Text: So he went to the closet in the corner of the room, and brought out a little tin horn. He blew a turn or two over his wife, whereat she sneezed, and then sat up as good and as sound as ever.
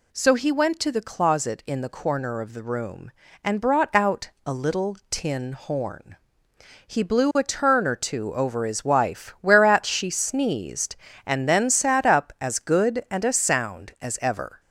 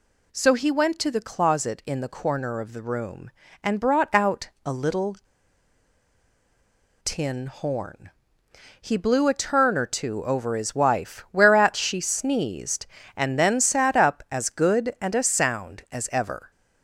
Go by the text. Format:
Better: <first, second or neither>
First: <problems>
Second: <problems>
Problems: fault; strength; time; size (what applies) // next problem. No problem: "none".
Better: first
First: none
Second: pauses between "little" and "tin"; strong; at 5.1 s; 1.8 s long